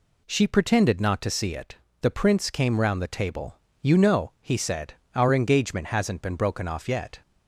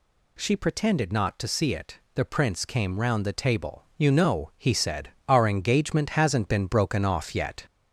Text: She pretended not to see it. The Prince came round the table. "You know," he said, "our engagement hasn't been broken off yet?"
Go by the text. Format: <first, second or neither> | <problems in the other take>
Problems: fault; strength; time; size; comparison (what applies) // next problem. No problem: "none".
first | gets louder; throughout; 3.5 dB